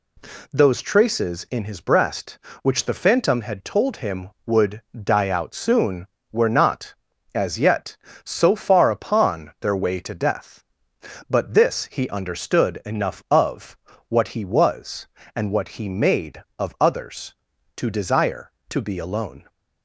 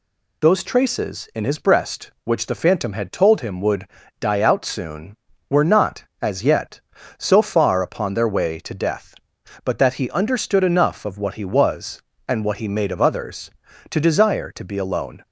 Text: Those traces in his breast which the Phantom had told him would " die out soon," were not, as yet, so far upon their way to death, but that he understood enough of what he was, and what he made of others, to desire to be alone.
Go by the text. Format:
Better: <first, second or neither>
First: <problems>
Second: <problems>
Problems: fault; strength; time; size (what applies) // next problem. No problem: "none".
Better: second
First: says "this" for "that"; at 11.5 s // pauses between "of" and "what"; slight; at 13.7 s; 0.32 s long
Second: none